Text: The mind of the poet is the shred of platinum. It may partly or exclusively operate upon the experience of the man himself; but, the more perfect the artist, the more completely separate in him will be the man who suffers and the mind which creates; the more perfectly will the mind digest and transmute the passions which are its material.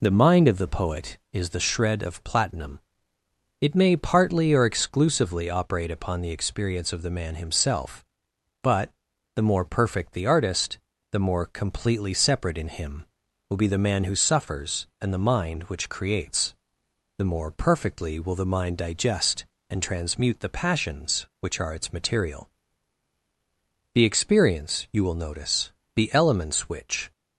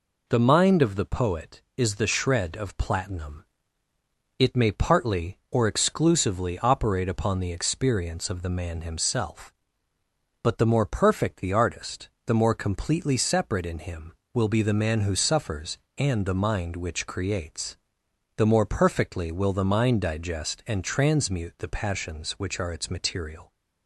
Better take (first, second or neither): second